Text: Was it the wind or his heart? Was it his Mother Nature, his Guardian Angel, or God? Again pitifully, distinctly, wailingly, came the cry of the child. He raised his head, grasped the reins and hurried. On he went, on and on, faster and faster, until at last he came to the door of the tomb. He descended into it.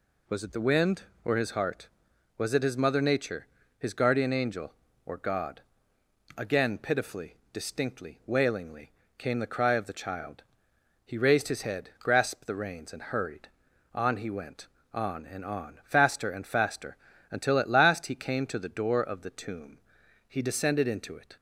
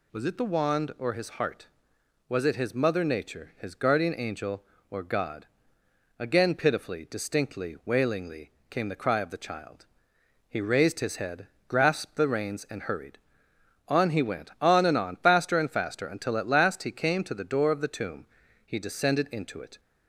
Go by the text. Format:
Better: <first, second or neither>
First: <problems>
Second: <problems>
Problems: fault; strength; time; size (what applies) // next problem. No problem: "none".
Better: first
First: none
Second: says "wand" for "wind"; at 0.4 s